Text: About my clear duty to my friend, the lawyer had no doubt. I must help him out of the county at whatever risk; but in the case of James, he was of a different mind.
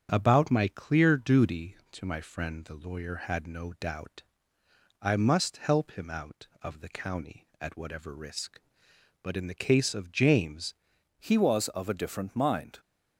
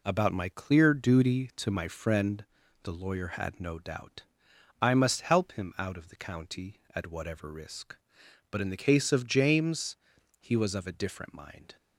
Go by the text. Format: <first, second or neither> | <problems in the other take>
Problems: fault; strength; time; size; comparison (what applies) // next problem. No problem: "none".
second | starts louder than the rest; strong; until 1.1 s; 7.5 dB // changes voice at "he"; from 11.1 s on; 1.6 s long